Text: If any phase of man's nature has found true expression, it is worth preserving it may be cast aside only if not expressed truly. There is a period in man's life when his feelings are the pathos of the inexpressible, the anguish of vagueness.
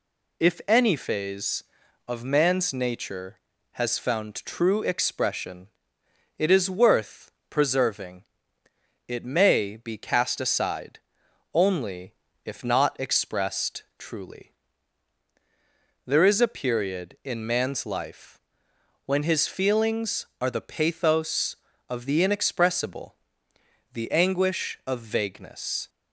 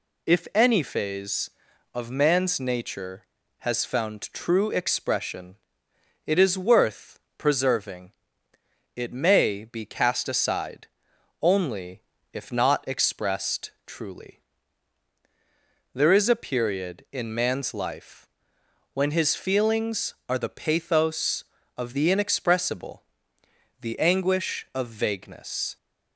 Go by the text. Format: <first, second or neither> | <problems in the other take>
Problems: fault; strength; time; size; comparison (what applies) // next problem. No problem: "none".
neither | pauses between "worth" and "preserving"; slight; the same in both // pauses between "preserving" and "it"; noticeable; the same in both // pauses between "aside" and "only"; noticeable; the same in both // pauses between "only" and "if"; slight; the same in both // pauses between "expressed" and "truly"; slight; the same in both // pauses between "life" and "when"; noticeable; the same in both